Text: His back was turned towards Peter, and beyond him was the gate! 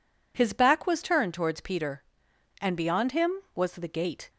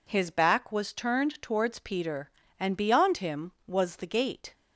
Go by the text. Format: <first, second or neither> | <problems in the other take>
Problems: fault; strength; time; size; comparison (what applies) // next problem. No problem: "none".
neither | none